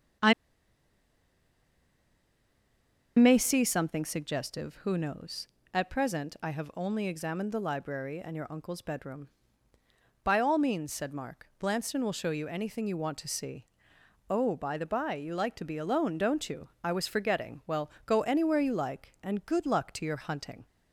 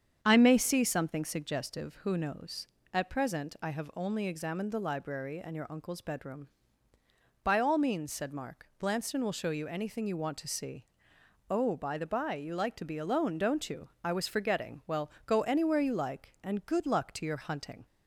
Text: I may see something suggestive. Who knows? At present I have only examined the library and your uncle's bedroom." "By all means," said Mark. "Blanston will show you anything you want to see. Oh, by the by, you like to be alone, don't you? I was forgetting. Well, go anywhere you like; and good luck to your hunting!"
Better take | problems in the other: second | starts louder than the rest; strong; until 4.0 s; 7.5 dB; strong in the second // pauses between "I" and "may"; strong; at 0.3 s; 2.8 s long

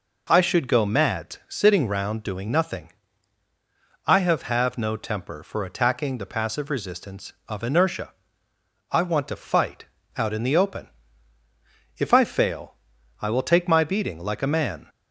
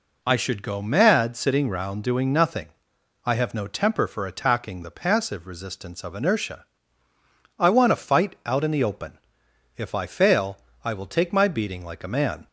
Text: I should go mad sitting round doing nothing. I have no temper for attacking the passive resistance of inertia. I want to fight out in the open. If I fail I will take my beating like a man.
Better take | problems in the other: second | says "have" twice; at 4.4 s // pauses between "fight" and "out"; slight; at 9.8 s; 0.32 s long // pauses between "fail" and "I"; noticeable; at 12.7 s; 0.48 s long; slight in the second

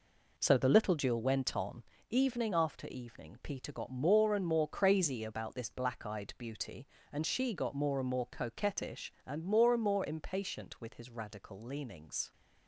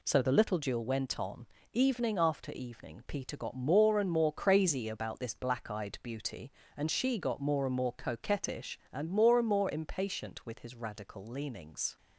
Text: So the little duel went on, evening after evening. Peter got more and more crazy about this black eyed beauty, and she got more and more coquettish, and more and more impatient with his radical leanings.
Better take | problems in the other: second | starts louder than the rest; noticeable; until 1.9 s; 4.5 dB

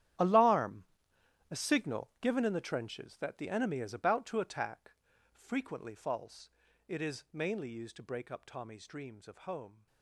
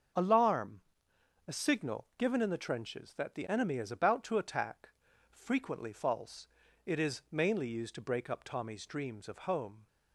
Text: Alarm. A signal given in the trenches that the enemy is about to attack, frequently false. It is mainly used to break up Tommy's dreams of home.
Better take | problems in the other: second | gets quieter; strong; throughout; 16.5 dB // starts louder than the rest; strong; until 1.8 s; 11 dB; also in the second

